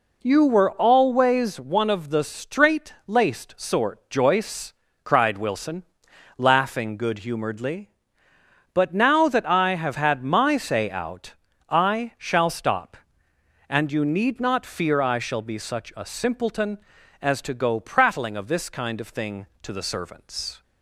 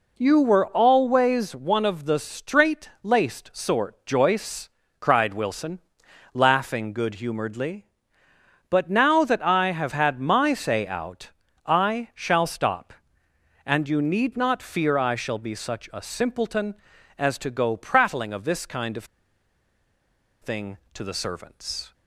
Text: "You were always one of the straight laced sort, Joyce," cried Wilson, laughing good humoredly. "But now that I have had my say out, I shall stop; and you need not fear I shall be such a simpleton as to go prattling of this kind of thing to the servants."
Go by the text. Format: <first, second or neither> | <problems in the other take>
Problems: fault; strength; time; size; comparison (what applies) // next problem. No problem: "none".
first | pauses between "of" and "thing"; strong; at 19.0 s; 1.3 s long